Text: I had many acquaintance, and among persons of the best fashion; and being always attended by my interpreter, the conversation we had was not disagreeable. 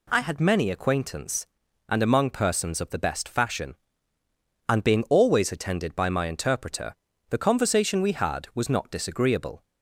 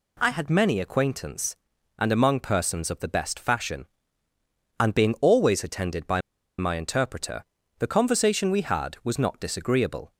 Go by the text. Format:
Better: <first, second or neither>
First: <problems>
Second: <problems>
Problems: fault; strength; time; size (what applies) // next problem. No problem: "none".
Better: first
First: none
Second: pauses between "by" and "my"; at 6.2 s; 0.38 s long